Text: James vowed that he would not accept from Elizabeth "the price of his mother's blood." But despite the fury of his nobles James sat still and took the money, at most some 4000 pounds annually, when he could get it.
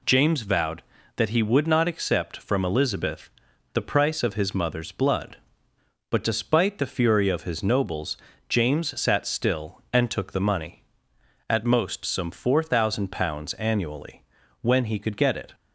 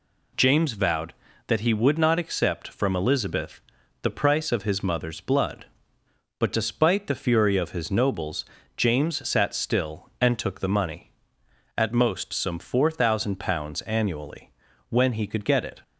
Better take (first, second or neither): neither